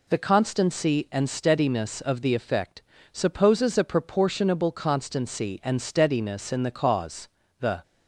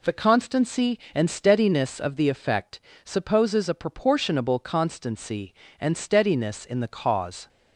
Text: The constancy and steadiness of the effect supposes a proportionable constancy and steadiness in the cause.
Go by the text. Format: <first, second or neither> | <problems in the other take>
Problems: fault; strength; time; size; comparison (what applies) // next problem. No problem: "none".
second | pauses between "effect" and "supposes"; slight; at 2.8 s; 0.32 s long; slight in the second // goes on to say "The"; slight; from 7.6 s on; 0.22 s long